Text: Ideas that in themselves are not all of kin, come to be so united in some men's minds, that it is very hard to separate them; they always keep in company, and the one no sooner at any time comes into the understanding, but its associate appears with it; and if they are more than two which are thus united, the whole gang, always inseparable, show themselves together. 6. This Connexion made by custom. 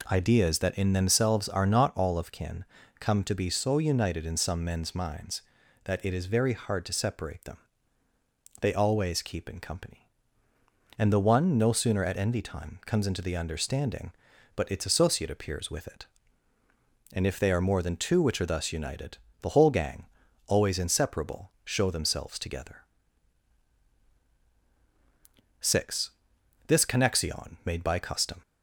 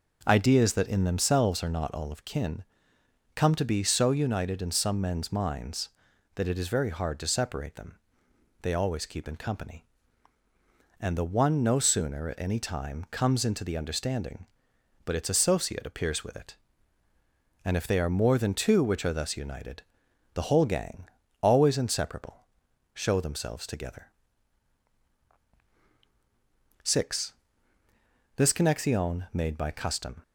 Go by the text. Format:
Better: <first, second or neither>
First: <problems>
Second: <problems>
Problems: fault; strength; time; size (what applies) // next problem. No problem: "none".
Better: second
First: says "envy" for "any"; at 12.1 s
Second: none